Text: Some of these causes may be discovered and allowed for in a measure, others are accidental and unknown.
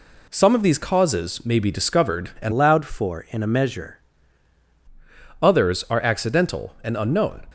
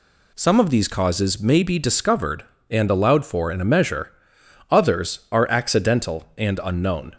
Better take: second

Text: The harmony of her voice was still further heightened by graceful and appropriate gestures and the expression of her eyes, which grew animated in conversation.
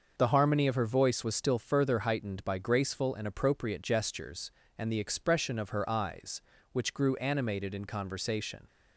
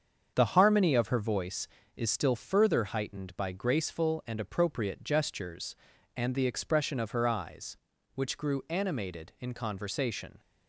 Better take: first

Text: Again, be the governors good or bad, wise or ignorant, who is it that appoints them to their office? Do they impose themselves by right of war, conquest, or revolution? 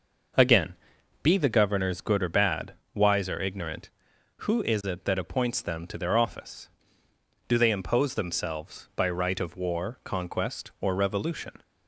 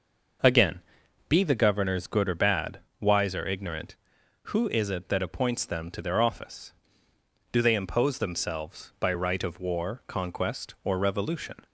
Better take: neither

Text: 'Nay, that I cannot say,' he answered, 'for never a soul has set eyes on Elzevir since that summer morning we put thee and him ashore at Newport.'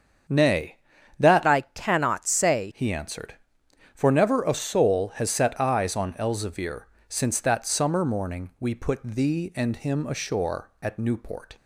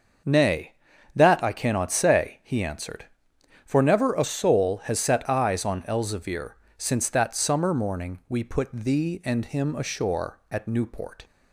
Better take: second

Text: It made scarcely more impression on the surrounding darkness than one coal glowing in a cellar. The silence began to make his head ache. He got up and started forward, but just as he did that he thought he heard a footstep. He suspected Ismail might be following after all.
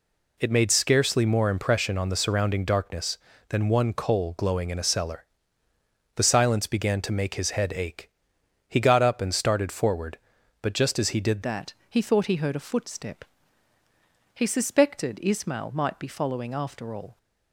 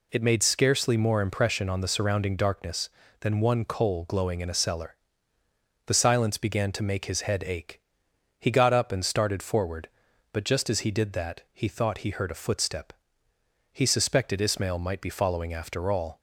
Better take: second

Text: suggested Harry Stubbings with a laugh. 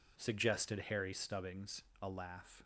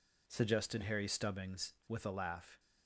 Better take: second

